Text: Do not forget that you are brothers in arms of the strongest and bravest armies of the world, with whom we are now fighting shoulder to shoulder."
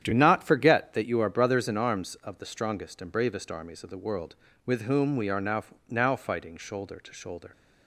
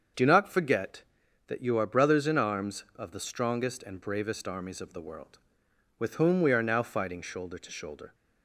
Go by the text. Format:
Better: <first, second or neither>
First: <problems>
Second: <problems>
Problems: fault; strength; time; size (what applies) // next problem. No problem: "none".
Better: second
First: starts louder than the rest; strong; until 1.0 s; 9.5 dB // says "now" twice; at 5.8 s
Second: starts louder than the rest; until 1.6 s; 7 dB